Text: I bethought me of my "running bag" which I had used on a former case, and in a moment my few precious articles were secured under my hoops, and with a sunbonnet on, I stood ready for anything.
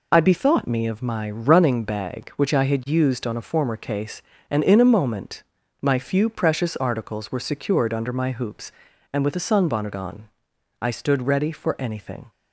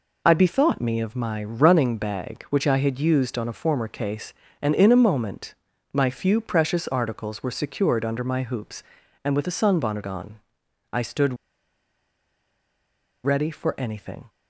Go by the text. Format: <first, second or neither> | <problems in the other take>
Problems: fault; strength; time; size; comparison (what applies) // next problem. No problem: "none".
first | pauses between "moment" and "my"; at 5.5 s; 0.40 s long; also in the first // pauses between "stood" and "ready"; strong; at 11.3 s; 1.8 s long